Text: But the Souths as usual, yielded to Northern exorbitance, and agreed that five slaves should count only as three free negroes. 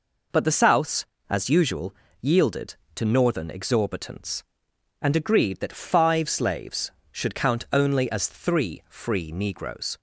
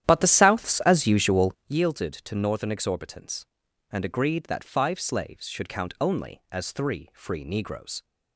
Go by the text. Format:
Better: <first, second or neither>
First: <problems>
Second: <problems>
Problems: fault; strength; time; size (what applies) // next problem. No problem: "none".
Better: first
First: none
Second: starts louder than the rest; strong; until 1.8 s; 11 dB